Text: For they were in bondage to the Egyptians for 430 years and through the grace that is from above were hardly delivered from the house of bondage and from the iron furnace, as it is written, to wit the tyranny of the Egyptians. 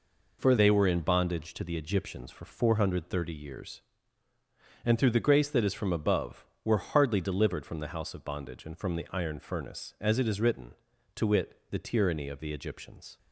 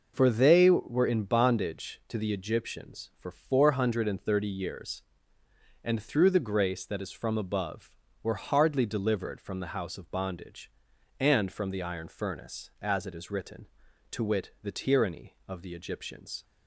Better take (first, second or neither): second